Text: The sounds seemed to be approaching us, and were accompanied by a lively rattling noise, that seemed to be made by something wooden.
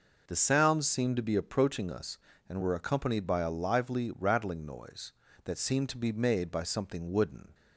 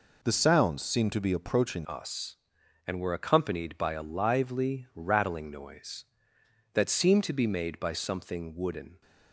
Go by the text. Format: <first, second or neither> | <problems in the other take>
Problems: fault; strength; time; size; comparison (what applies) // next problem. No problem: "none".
first | changes voice at "us"; from 1.8 s on; 7.2 s long